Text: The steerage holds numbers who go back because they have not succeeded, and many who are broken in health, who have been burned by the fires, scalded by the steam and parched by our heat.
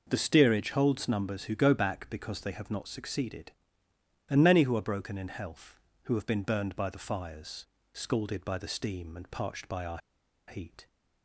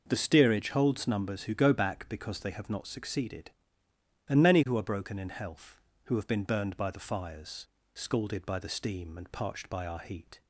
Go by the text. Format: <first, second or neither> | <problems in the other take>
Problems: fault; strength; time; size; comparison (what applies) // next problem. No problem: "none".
second | pauses between "our" and "heat"; noticeable; at 9.9 s; 0.50 s long